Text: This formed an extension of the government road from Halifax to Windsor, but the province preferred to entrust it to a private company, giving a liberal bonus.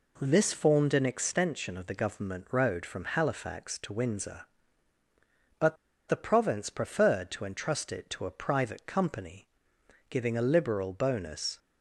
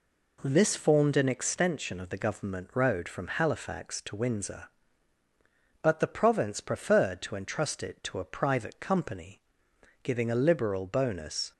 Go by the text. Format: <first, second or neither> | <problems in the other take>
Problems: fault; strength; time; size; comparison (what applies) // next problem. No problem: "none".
second | pauses between "but" and "the"; slight; at 5.7 s; 0.32 s long